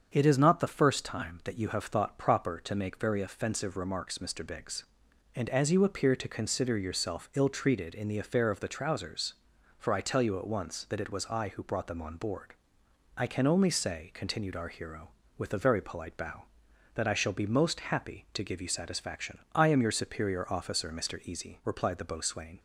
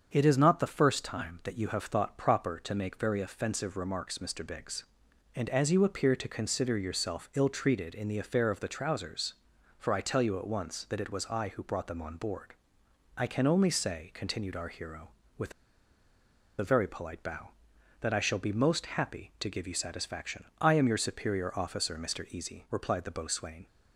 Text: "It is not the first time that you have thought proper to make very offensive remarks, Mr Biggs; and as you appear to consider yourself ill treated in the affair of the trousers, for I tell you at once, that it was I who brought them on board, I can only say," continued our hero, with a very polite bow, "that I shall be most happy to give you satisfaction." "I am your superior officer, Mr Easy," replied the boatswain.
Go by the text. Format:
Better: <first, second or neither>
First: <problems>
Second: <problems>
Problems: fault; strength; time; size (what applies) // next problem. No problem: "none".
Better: first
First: starts louder than the rest; strong; until 1.1 s; 7 dB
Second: starts louder than the rest; strong; until 1.1 s; 7 dB // pauses between "with" and "a"; at 15.5 s; 1.0 s long